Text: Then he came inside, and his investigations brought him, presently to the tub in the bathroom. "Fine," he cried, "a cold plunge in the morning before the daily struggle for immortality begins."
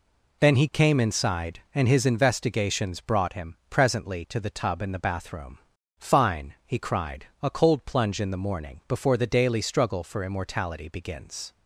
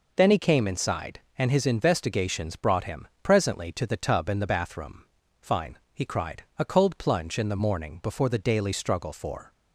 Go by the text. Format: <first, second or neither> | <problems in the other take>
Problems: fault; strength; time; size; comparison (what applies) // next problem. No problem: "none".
first | stops before "immortality begins"; at 9.5 s